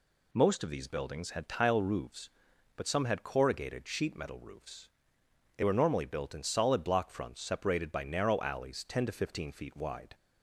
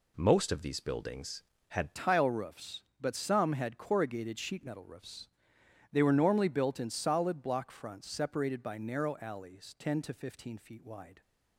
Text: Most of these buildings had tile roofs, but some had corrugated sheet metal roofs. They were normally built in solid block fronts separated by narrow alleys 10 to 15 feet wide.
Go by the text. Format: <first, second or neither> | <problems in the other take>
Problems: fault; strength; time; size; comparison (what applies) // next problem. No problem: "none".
first | changes voice at "tile"; from 1.9 s on; 9.3 s long